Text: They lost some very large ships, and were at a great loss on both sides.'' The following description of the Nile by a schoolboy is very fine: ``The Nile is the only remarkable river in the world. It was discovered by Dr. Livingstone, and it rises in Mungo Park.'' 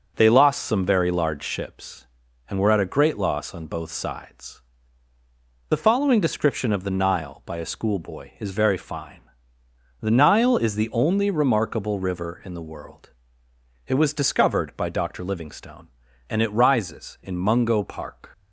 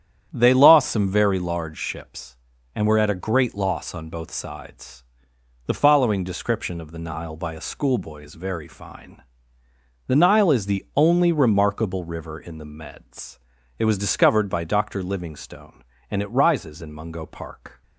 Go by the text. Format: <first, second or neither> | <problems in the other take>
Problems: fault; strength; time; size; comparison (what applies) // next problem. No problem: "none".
first | starts louder than the rest; strong; until 1.3 s; 9.5 dB // says "meds" for "world"; at 12.6 s